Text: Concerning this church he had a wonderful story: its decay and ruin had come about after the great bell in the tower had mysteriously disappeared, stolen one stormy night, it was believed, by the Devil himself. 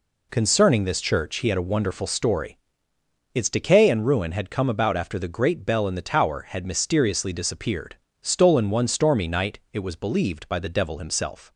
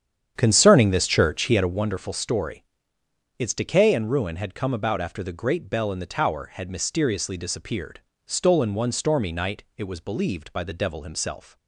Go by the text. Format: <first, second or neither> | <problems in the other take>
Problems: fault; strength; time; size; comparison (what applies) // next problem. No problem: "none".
first | starts louder than the rest; strong; until 1.9 s; 8.5 dB